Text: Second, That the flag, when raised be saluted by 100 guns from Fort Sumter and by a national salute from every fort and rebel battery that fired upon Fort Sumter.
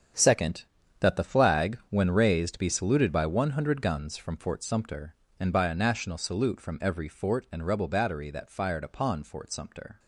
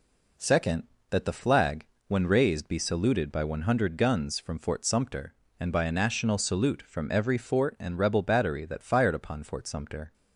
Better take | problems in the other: second | gets quieter; strong; throughout; 12 dB

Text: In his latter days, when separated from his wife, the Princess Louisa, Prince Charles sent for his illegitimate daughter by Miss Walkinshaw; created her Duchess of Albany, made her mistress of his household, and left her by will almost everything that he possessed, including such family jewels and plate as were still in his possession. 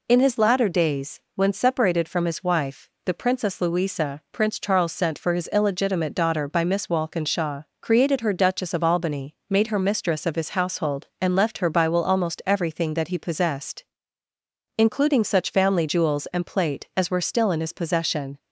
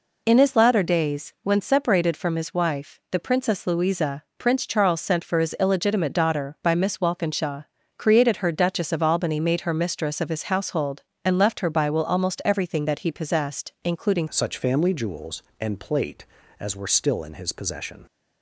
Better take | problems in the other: first | changes voice at "such"; from 14.2 s on; 3.8 s long

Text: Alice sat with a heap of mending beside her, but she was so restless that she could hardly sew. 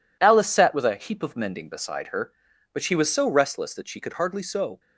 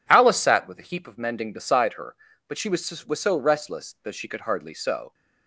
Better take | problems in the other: first | says "was" twice; at 3.0 s

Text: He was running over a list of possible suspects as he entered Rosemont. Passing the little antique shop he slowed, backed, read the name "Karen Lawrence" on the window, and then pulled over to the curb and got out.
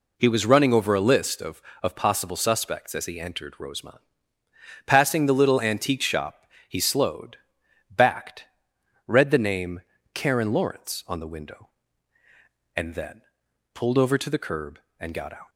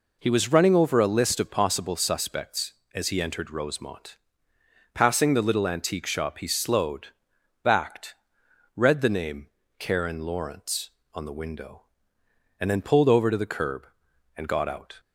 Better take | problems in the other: second | says "of" twice; at 1.8 s // pauses between "shop" and "he"; slight; at 6.4 s; 0.24 s long // pauses between "name" and "Karen"; slight; at 9.8 s; 0.34 s long; slight in the second // pauses between "then" and "pulled"; noticeable; at 13.2 s; 0.54 s long

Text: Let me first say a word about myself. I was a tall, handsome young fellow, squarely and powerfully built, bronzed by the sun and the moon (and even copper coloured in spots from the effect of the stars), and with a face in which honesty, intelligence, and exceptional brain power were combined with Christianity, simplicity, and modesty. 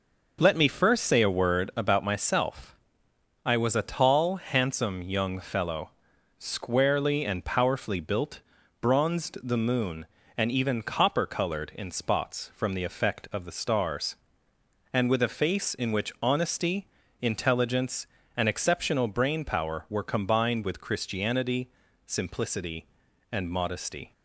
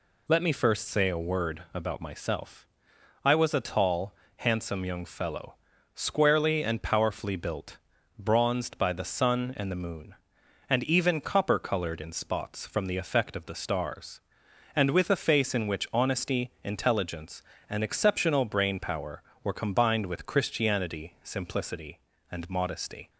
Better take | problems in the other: second | skips "by the sun and"; at 9.3 s

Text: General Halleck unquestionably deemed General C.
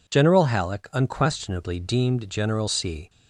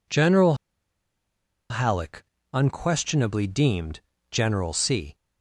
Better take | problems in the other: first | pauses between "General" and "Halleck"; at 0.5 s; 1.1 s long // pauses between "Halleck" and "unquestionably"; slight; at 2.2 s; 0.28 s long // pauses between "deemed" and "General"; slight; at 3.9 s; 0.32 s long

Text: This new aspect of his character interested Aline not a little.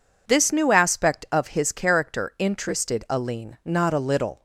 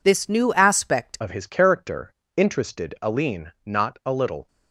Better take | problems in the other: first | changes voice at "of"; from 1.1 s on; 3.3 s long // pauses between "character" and "interested"; slight; at 2.1 s; 0.24 s long

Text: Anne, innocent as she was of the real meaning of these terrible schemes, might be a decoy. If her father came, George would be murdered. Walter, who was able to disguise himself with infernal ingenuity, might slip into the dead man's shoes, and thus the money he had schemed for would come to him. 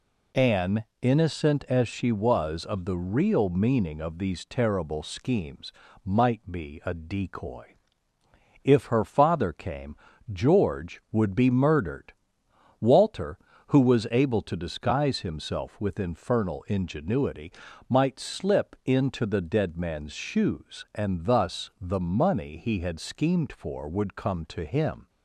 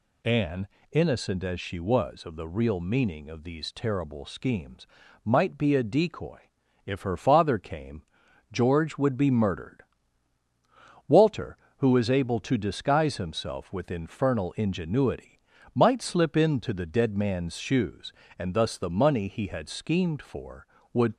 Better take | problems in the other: first | stops before "come to him"; at 21.1 s

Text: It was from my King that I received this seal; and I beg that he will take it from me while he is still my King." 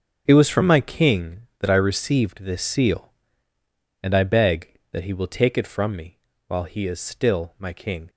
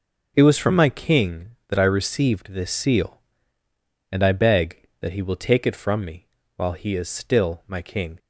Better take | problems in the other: second | gets quieter; strong; throughout; 12.5 dB // pauses between "me" and "while"; slight; at 6.1 s; 0.30 s long; slight in the second

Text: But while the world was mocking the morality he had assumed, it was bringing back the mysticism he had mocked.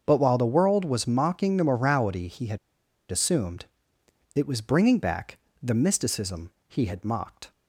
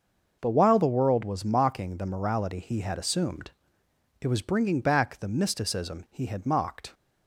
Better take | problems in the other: second | starts louder than the rest; until 1.0 s; 6.5 dB // pauses between "had" and "assumed"; noticeable; at 2.5 s; 0.53 s long // pauses between "back" and "the"; slight; at 5.3 s; 0.24 s long // pauses between "mysticism" and "he"; slight; at 6.5 s; 0.16 s long

